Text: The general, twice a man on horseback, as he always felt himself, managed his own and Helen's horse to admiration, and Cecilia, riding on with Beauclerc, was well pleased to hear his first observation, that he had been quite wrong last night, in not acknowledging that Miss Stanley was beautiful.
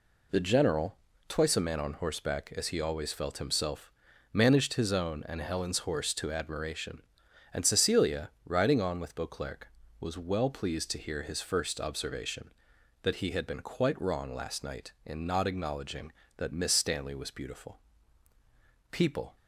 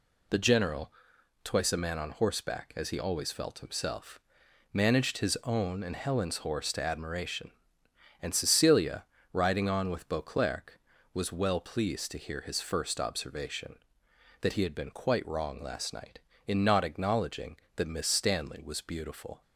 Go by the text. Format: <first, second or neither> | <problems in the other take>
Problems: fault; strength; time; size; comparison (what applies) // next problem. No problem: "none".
second | goes on to say "People"; slight; from 18.9 s on; 0.44 s long